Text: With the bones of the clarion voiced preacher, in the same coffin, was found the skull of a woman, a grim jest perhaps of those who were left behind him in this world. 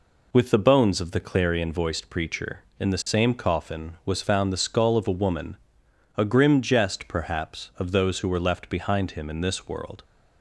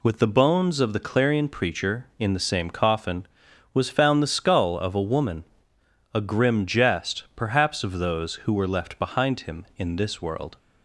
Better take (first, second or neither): first